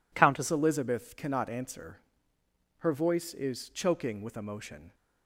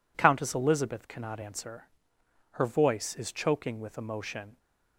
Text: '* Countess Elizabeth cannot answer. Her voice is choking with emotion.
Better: second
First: changes voice at "Elizabeth"; from 0.5 s on; 4.4 s long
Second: none

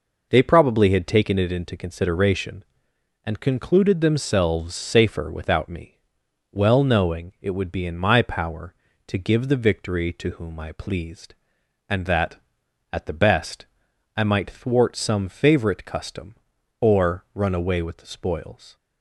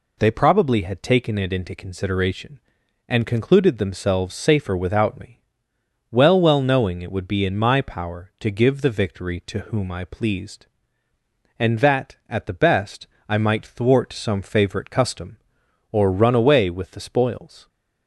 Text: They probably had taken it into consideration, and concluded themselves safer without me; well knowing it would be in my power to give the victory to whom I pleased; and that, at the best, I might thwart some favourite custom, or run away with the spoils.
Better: first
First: none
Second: says "well" twice; at 6.4 s

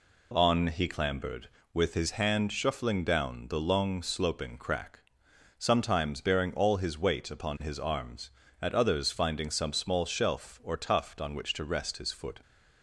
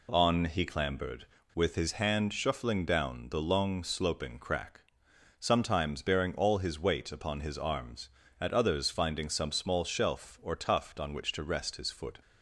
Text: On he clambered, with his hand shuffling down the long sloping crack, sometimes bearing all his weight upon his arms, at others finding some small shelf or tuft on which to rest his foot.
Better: neither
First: none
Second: none

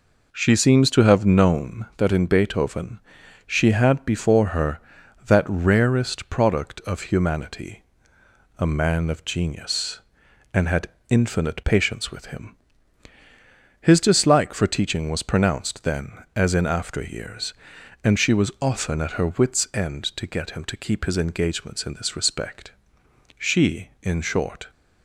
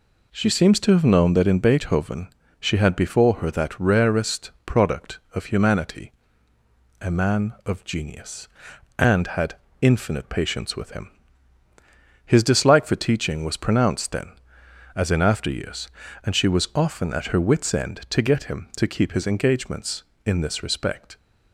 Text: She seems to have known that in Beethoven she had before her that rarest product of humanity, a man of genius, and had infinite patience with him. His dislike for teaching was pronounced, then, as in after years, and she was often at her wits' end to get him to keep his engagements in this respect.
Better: second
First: pauses between "Beethoven" and "she"; noticeable; at 3.0 s; 0.46 s long // pauses between "had" and "infinite"; slight; at 10.8 s; 0.20 s long // goes on to say "She in short"; from 23.3 s on; 1.3 s long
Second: pauses between "Beethoven" and "she"; slight; at 2.2 s; 0.30 s long // pauses between "had" and "infinite"; slight; at 9.5 s; 0.24 s long

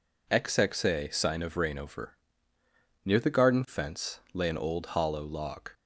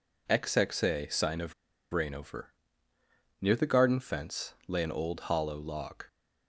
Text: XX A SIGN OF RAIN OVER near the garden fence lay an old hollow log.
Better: first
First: pauses between "OVER" and "near"; noticeable; at 2.1 s; 0.88 s long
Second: pauses between "OF" and "RAIN"; at 1.5 s; 0.37 s long // pauses between "OVER" and "near"; noticeable; at 2.5 s; 0.88 s long

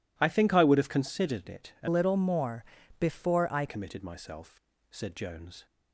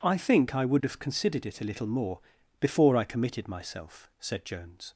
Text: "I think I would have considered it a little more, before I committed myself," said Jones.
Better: second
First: changes voice from "little" to "I"; from 1.8 to 3.6 s; 1.8 s long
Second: none

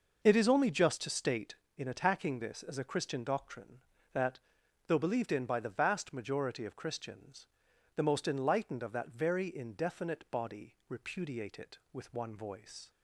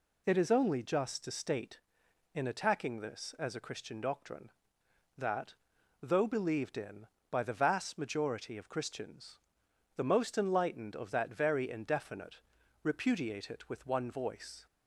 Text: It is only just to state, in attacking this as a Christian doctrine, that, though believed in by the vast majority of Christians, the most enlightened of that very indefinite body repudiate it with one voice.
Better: first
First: none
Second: skips "body"; at 12.6 s

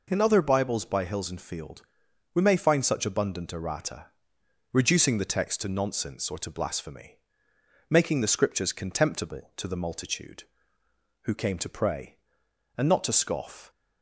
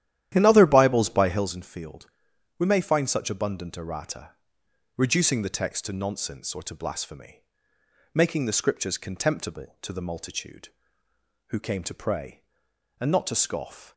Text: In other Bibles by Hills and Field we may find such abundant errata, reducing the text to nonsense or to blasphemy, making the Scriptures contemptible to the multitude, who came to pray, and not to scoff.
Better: first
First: pauses between "Field" and "we"; noticeable; at 1.8 s; 0.50 s long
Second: starts louder than the rest; strong; until 1.6 s; 11.5 dB // pauses between "Field" and "we"; noticeable; at 2.0 s; 0.50 s long

